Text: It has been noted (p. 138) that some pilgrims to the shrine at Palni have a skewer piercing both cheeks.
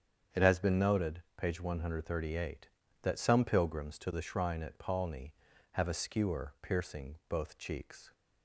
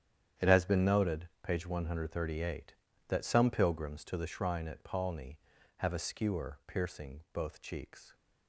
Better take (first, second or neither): first